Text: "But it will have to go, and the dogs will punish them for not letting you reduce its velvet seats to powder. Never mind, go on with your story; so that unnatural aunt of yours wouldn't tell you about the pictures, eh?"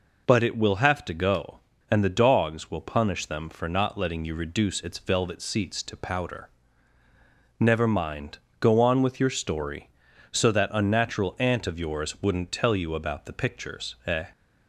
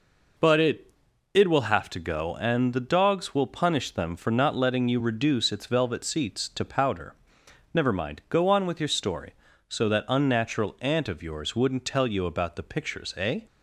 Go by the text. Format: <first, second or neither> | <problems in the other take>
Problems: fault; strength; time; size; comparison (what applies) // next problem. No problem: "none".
first | says "it" twice; at 1.3 s